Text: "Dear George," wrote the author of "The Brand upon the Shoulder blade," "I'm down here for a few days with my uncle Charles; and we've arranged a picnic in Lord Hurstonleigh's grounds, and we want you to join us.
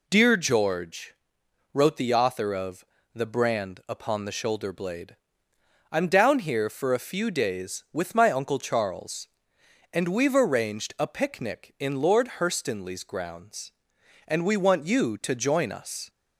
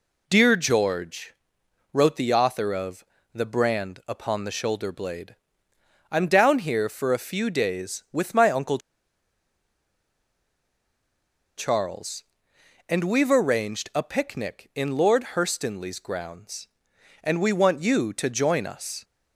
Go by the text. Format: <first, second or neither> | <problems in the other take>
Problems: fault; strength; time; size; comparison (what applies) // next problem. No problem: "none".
first | pauses between "of" and "The"; slight; at 3.0 s; 0.28 s long; slight in the first // pauses between "uncle" and "Charles"; strong; at 8.7 s; 2.7 s long